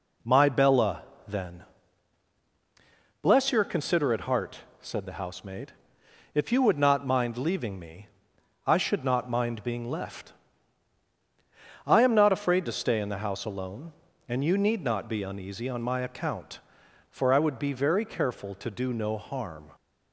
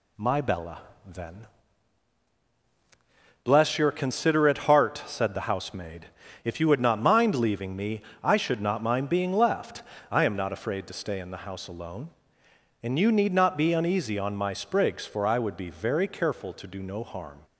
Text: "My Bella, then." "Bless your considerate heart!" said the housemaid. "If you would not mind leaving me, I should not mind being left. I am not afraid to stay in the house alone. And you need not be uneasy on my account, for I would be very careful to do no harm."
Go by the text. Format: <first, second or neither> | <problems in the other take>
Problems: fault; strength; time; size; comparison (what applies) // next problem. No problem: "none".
first | says "sprigs" for "account"; at 14.5 s